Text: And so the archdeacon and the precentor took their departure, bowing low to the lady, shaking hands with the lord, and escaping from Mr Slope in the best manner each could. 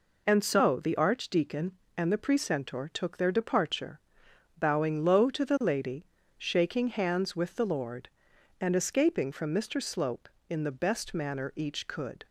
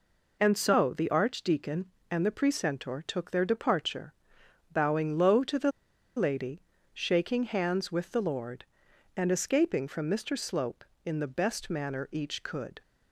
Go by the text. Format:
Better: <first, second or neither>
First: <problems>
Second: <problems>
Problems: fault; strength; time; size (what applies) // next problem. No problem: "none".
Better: first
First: none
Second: pauses between "the" and "lady"; noticeable; at 5.7 s; 0.46 s long